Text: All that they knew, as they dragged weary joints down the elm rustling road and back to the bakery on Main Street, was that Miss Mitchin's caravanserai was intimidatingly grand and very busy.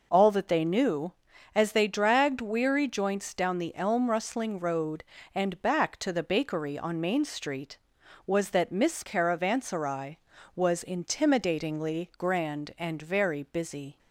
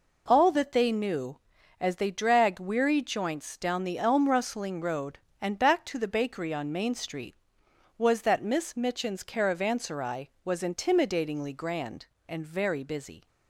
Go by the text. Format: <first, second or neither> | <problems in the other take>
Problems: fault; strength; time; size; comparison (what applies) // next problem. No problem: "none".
second | skips "Mitchin's"; at 9.0 s